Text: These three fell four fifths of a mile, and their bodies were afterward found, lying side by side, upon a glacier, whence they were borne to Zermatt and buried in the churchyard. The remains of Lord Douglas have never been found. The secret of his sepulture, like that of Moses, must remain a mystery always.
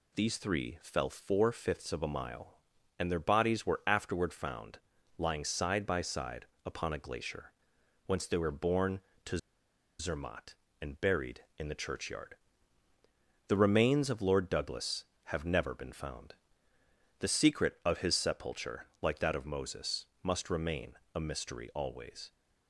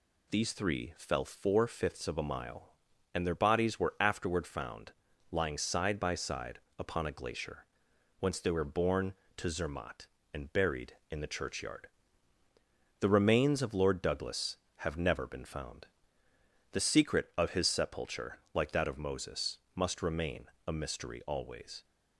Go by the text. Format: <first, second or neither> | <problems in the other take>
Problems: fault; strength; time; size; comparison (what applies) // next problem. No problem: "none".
second | pauses between "to" and "Zermatt"; noticeable; at 9.3 s; 0.60 s long // pauses between "remain" and "a"; slight; at 20.9 s; 0.18 s long; slight in the second